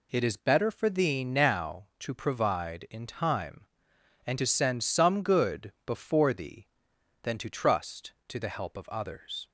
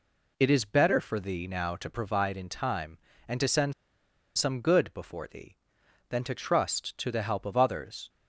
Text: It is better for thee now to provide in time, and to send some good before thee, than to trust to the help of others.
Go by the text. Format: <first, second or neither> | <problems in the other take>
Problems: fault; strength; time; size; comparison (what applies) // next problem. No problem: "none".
first | pauses between "send" and "some"; noticeable; at 3.7 s; 0.65 s long